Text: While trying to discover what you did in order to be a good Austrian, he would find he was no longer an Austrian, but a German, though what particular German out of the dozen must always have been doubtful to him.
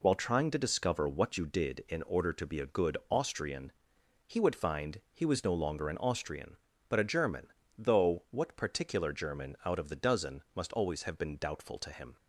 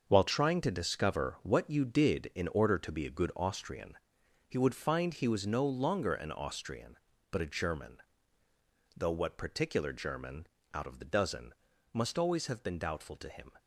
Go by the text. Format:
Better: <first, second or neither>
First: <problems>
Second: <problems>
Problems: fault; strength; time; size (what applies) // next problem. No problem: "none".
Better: first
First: none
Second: gets quieter; strong; throughout; 9 dB // pauses between "German" and "out"; slight; at 10.4 s; 0.26 s long // pauses between "dozen" and "must"; at 11.5 s; 0.38 s long